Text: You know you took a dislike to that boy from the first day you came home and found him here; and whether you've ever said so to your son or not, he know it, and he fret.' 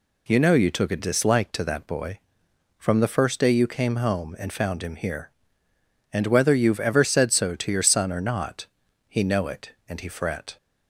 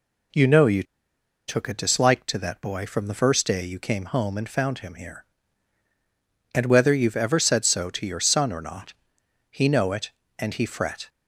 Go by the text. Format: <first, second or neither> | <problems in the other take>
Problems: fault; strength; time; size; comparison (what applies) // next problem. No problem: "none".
first | pauses between "you" and "took"; noticeable; at 0.8 s; 0.63 s long